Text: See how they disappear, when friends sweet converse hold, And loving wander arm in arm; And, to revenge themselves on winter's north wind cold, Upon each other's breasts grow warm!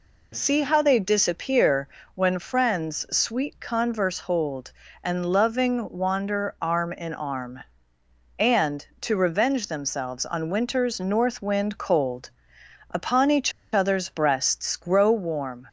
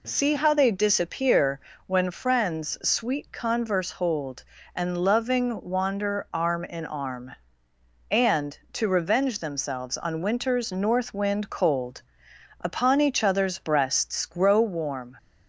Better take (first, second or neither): second